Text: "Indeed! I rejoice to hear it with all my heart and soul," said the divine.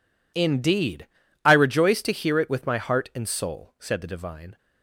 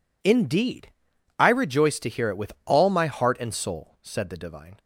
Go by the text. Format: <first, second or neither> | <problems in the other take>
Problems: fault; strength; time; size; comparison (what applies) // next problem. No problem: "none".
second | skips "all"; at 2.6 s